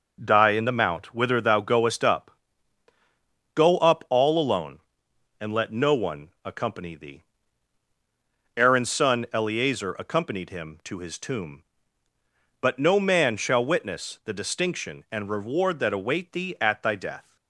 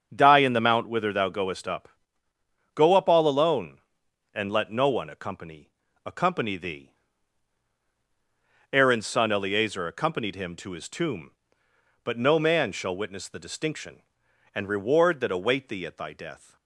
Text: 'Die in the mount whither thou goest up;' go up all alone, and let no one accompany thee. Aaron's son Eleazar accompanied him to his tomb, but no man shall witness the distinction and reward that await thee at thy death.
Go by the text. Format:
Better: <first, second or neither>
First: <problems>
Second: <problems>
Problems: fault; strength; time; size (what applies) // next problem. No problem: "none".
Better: first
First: none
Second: starts louder than the rest; strong; until 1.1 s; 7 dB // says "accompany" twice; at 6.0 s